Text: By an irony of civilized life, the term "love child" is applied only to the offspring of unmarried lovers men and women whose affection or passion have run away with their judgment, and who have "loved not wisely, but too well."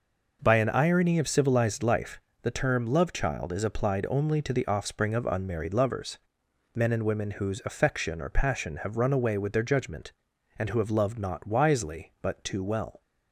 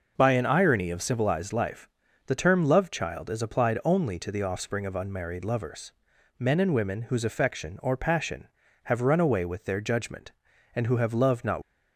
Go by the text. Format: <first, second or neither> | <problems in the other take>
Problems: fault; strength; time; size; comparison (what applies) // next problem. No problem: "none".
first | pauses between "lovers" and "men"; noticeable; at 5.9 s; 0.48 s long; noticeable in the first // stops before "wisely but too well"; at 11.6 s